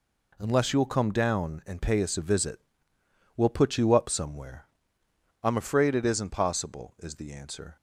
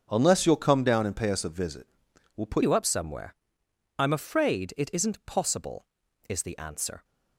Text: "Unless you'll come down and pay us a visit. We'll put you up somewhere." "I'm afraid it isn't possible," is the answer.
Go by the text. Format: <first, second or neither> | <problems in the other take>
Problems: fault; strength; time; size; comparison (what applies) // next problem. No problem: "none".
first | starts louder than the rest; until 1.1 s; 7 dB // changes voice at "you"; from 2.6 s on; 4.4 s long